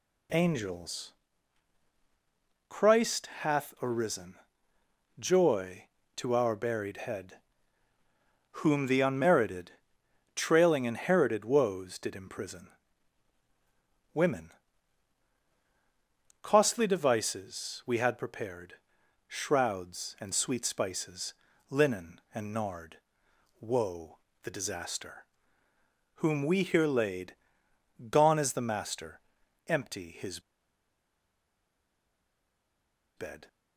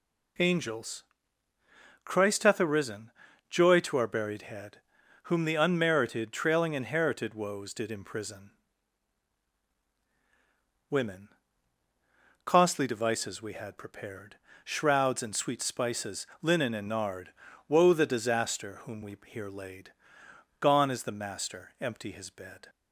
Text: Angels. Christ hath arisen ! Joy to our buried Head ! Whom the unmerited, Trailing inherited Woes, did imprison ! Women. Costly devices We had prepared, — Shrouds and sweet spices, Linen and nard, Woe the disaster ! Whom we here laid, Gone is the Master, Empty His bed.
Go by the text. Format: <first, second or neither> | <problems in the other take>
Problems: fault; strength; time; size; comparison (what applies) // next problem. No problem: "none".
second | pauses between "Woe" and "the"; slight; at 24.1 s; 0.24 s long // pauses between "His" and "bed"; strong; at 30.4 s; 2.7 s long